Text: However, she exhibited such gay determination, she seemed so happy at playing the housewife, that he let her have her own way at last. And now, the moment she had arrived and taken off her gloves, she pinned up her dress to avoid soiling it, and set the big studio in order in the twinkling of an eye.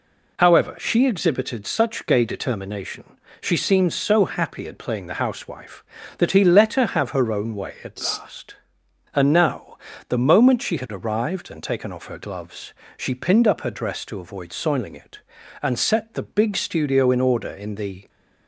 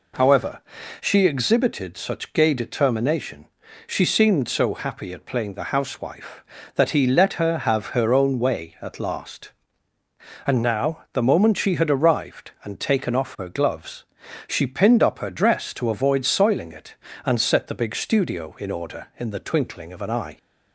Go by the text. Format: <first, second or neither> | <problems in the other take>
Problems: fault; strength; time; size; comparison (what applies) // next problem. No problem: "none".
second | stops before "twinkling of an eye"; at 18.0 s